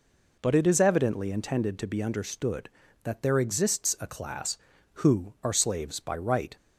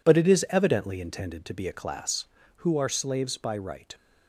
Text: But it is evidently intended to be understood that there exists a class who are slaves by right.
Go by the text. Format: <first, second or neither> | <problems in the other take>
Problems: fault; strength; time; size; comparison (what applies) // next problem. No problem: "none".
first | skips "understood that there exists"; at 1.6 s